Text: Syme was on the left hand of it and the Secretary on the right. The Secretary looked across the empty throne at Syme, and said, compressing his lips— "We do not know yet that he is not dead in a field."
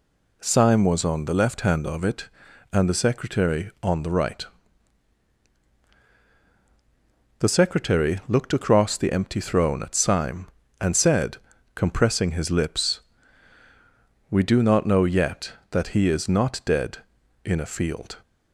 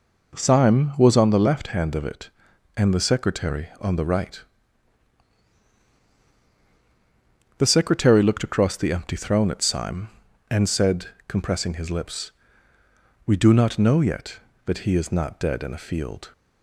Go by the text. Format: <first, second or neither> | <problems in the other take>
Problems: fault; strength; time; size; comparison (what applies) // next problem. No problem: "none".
neither | none